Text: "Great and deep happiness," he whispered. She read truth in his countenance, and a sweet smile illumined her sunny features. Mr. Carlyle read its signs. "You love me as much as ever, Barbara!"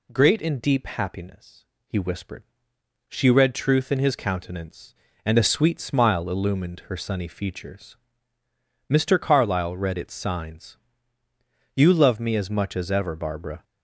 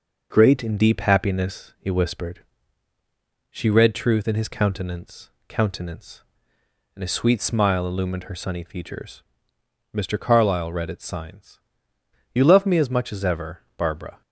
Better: first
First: none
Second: says "countenance" twice; at 5.4 s

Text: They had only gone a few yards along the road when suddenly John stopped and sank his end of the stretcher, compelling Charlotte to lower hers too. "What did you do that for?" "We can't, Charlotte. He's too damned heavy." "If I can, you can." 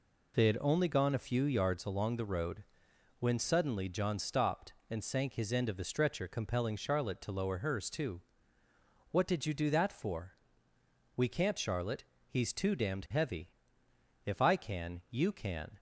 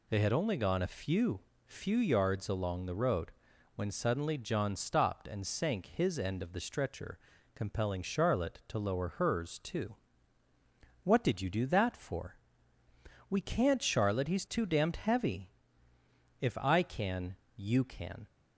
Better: first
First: pauses between "road" and "when"; noticeable; at 2.6 s; 0.56 s long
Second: says "few" twice; at 1.6 s // pauses between "road" and "when"; noticeable; at 3.2 s; 0.46 s long

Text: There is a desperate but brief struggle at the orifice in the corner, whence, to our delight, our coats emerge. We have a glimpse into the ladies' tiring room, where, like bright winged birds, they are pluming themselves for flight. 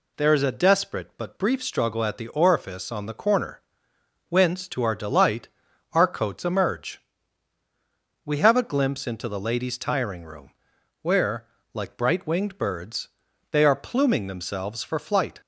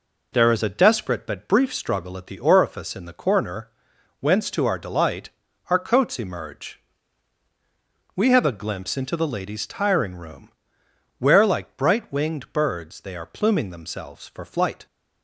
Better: second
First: says "on" for "in"; at 2.9 s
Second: none

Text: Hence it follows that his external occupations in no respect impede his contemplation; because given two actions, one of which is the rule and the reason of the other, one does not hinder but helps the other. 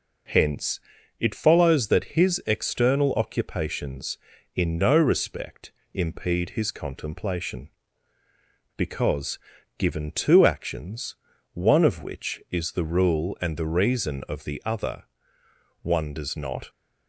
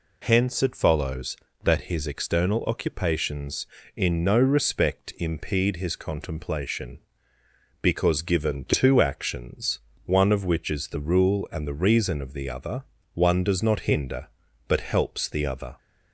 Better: second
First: pauses between "Hence" and "it"; at 0.8 s; 0.40 s long // pauses between "respect" and "impede"; slight; at 5.7 s; 0.22 s long // pauses between "because" and "given"; at 9.3 s; 0.38 s long // stops before "hinder but helps the other"; at 16.6 s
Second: none

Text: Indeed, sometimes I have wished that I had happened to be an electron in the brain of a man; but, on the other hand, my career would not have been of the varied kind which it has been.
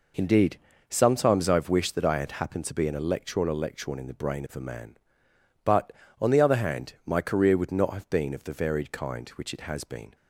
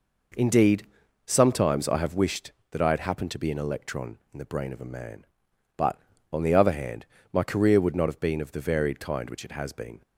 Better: second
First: says "electron" twice; at 3.4 s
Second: none

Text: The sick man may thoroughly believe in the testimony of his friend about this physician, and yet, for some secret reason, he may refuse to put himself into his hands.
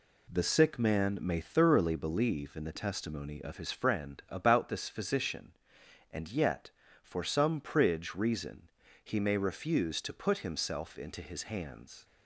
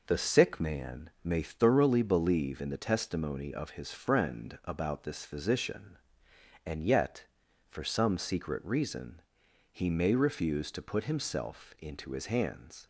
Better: second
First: says "pridge" for "secret"; at 7.6 s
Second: none

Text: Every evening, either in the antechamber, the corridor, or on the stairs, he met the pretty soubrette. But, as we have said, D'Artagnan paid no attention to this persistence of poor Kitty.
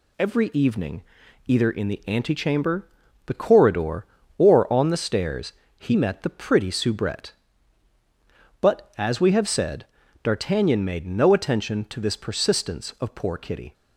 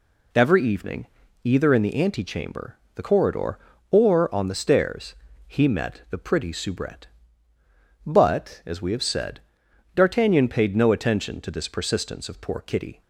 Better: second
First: says "made" for "paid"; at 10.8 s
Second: none

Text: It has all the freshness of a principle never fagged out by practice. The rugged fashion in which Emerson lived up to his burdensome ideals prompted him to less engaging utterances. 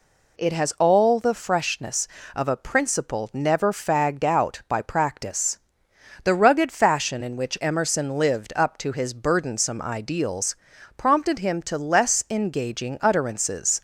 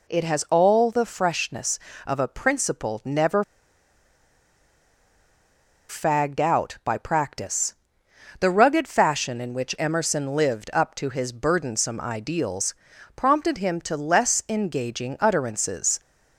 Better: first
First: pauses between "ideals" and "prompted"; at 10.5 s; 0.42 s long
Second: pauses between "never" and "fagged"; strong; at 3.4 s; 2.4 s long // pauses between "ideals" and "prompted"; at 12.7 s; 0.42 s long

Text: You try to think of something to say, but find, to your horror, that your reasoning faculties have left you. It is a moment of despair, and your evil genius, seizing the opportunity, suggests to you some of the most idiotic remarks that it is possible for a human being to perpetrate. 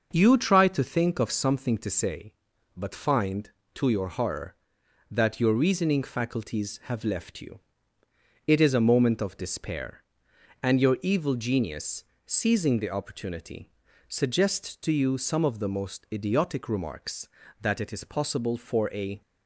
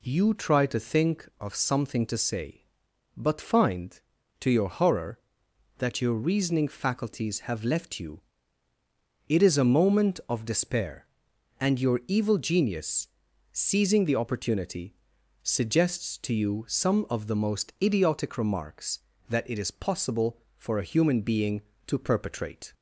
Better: second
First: starts louder than the rest; until 1.1 s; 6 dB // stops before "human being to perpetrate"; at 19.2 s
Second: none

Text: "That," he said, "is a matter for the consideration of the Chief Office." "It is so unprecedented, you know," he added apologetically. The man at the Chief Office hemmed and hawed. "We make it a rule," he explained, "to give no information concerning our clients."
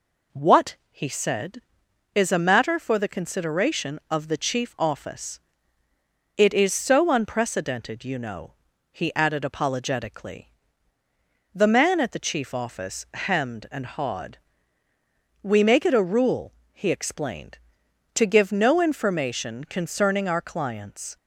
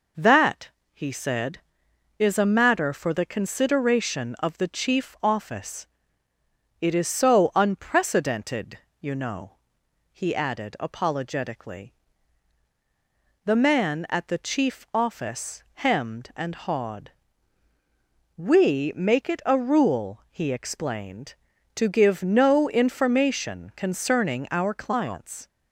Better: second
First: says "What" for "That"; at 0.3 s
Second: none

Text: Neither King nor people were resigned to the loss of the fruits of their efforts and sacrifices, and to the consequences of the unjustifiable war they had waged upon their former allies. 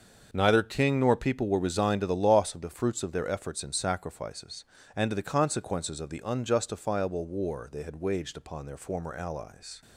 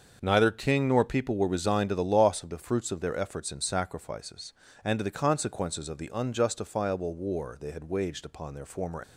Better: first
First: starts louder than the rest; until 1.3 s; 7 dB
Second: starts louder than the rest; until 1.2 s; 7 dB // stops before "allies"; at 9.0 s

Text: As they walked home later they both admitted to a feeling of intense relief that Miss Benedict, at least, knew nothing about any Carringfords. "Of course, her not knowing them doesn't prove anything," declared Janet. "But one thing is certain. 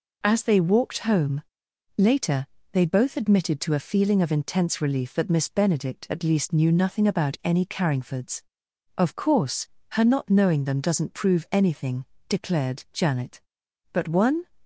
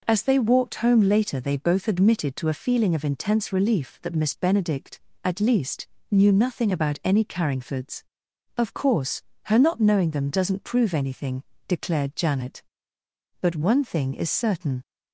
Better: second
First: pauses between "home" and "later"; noticeable; at 1.4 s; 0.56 s long // pauses between "later" and "they"; slight; at 2.4 s; 0.26 s long // stops before "thing is certain"; at 14.6 s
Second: none

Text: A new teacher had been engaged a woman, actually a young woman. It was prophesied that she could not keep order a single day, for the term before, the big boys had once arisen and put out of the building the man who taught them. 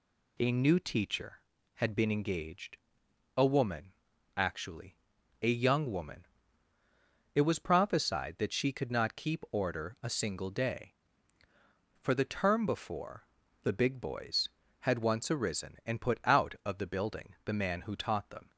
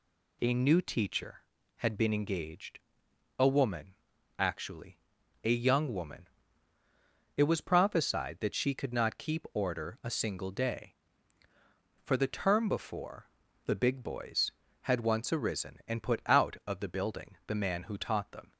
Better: neither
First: pauses between "engaged" and "a"; noticeable; at 2.7 s; 0.60 s long // pauses between "actually" and "a"; noticeable; at 4.9 s; 0.46 s long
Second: pauses between "engaged" and "a"; noticeable; at 2.7 s; 0.60 s long // pauses between "actually" and "a"; noticeable; at 4.9 s; 0.46 s long

